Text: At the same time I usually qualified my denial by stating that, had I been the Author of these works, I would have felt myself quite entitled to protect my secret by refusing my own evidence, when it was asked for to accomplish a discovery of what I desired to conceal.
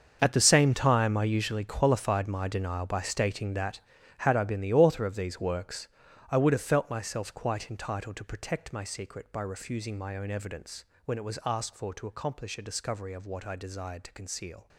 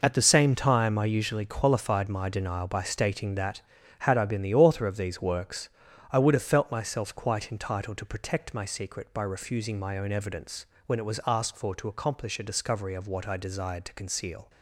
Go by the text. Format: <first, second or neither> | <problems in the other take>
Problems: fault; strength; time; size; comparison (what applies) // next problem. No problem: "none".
second | gets quieter; strong; throughout; 14.5 dB